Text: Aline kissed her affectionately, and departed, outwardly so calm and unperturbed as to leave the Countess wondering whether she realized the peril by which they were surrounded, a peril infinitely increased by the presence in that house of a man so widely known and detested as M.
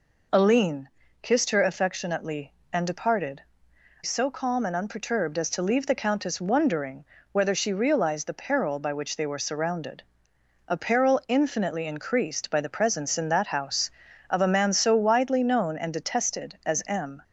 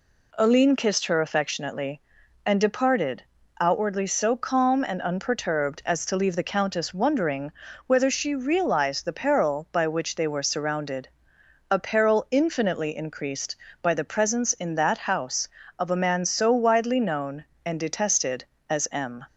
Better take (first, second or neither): second